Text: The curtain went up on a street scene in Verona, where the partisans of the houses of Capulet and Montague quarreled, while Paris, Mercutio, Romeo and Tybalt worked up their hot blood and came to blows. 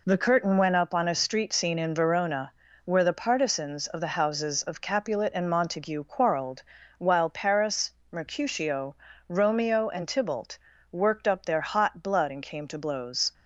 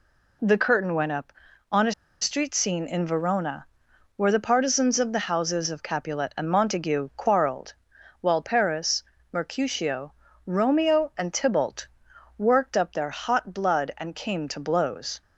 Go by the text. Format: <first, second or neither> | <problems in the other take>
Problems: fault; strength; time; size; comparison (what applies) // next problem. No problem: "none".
first | pauses between "a" and "street"; slight; at 1.9 s; 0.29 s long // pauses between "Tybalt" and "worked"; noticeable; at 11.8 s; 0.50 s long; slight in the first